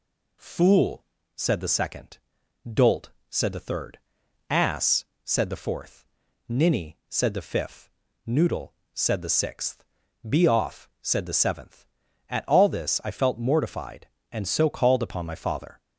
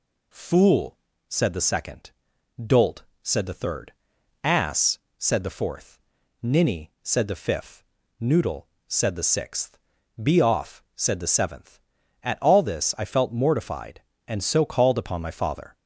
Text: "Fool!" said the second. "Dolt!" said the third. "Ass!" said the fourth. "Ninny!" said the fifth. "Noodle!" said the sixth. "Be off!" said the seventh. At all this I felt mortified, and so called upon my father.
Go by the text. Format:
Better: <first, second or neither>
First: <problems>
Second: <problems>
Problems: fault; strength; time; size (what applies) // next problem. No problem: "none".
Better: neither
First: none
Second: none